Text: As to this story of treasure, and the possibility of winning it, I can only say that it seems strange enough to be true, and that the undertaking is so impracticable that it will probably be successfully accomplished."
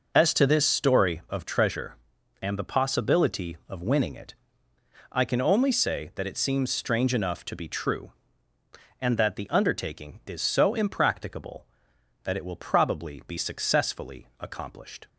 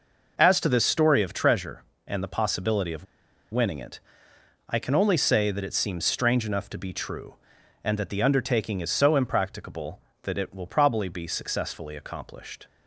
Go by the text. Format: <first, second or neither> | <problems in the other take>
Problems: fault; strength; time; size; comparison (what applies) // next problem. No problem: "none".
first | pauses between "of" and "winning"; noticeable; at 3.0 s; 0.46 s long